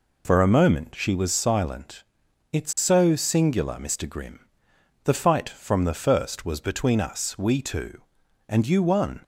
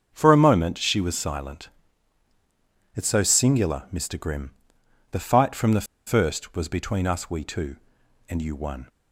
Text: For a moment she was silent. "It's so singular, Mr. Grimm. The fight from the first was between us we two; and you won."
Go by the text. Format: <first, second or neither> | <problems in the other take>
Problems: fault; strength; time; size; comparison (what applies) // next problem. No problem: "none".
first | starts louder than the rest; until 1.1 s; 7 dB // pauses between "the" and "first"; slight; at 5.8 s; 0.20 s long